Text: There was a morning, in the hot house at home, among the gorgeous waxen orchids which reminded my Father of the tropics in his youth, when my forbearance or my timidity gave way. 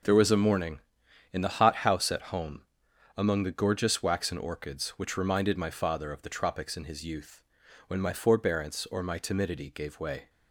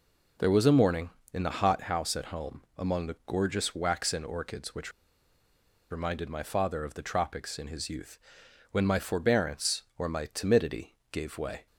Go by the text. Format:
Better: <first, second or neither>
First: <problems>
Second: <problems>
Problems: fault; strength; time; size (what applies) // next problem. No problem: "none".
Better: first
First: none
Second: pauses between "which" and "reminded"; at 4.9 s; 1.0 s long // pauses between "timidity" and "gave"; slight; at 10.9 s; 0.18 s long